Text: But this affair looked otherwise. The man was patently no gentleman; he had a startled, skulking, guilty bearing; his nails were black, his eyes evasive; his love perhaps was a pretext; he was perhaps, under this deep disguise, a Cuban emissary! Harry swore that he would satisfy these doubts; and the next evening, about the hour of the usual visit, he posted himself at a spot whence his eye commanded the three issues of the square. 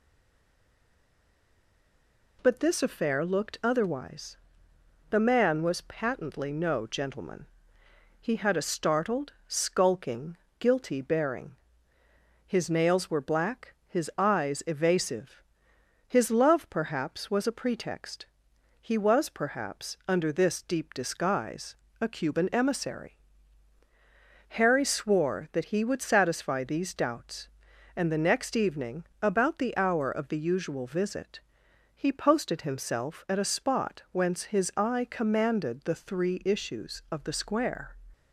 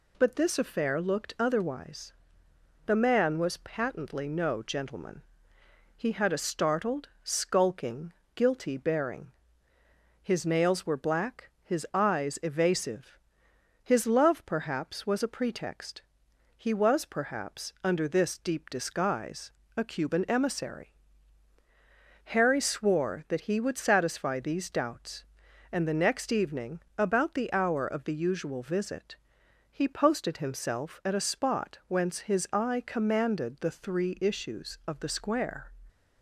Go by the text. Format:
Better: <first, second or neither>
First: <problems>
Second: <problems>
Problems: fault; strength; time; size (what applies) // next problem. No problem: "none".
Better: second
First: stays silent before the first word; until 2.3 s; 2.3 s long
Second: none